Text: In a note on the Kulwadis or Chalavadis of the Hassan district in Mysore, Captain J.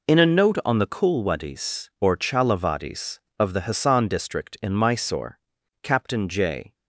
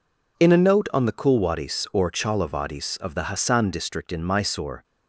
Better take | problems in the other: first | stops before "Captain J"; at 4.8 s

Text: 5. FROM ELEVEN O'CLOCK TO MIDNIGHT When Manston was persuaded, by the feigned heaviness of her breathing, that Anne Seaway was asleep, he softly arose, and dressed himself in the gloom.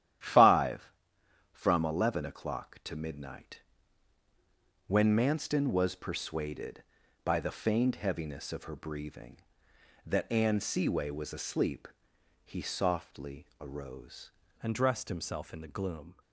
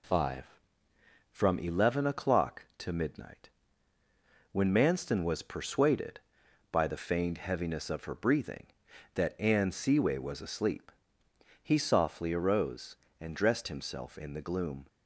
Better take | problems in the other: second | starts louder than the rest; strong; until 1.8 s; 11.5 dB // pauses between "MIDNIGHT" and "When"; strong; at 3.5 s; 1.2 s long; also in the second // changes voice at "and"; from 14.6 s on; 1.5 s long

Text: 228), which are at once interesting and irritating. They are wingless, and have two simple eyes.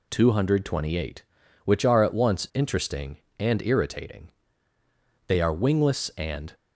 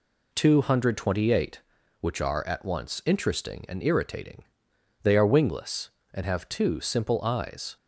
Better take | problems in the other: second | stops before "have two simple eyes"; at 6.5 s

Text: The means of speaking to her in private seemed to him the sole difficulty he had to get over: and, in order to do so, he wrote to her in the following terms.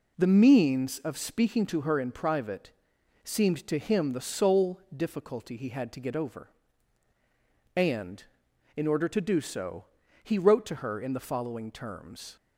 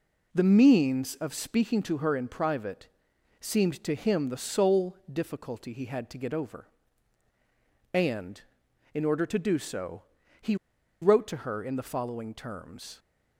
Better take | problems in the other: first | pauses between "private" and "seemed"; noticeable; at 2.8 s; 0.54 s long; noticeable in the first // pauses between "he" and "wrote"; noticeable; at 10.5 s; 0.46 s long

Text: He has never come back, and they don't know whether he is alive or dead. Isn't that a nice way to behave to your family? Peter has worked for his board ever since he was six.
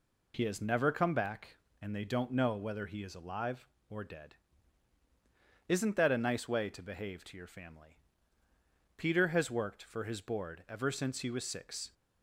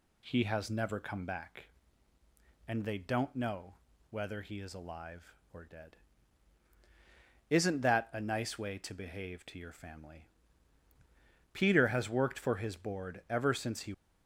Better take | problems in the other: first | pauses between "know" and "whether"; slight; at 3.7 s; 0.36 s long // stops before "was six"; at 13.9 s

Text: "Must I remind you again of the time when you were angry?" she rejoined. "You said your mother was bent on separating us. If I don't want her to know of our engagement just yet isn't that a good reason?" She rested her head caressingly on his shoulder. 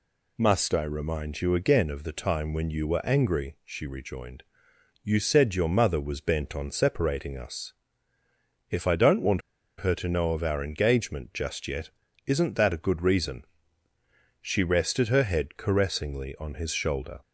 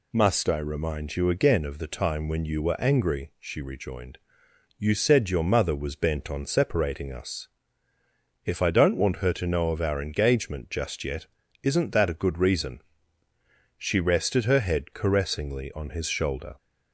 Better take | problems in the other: second | pauses between "want" and "her"; at 9.4 s; 0.38 s long // pauses between "yet" and "isn't"; at 11.8 s; 0.38 s long; also in the second

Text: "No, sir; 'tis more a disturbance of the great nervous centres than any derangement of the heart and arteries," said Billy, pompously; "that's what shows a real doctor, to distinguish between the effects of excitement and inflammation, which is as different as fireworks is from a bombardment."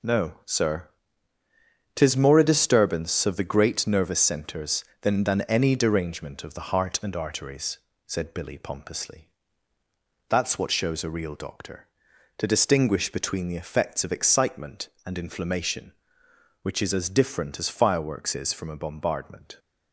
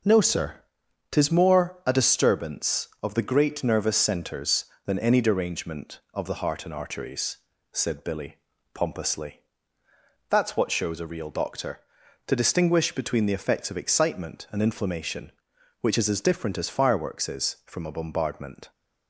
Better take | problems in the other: second | says "than" twice; at 5.2 s

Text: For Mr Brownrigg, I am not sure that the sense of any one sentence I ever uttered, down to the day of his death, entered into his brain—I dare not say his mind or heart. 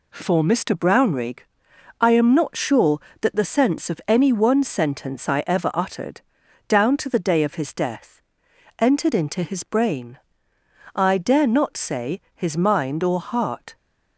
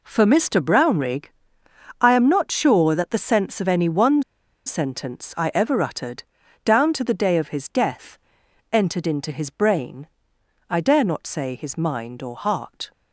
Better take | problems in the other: first | pauses between "one" and "sentence"; at 4.2 s; 0.44 s long

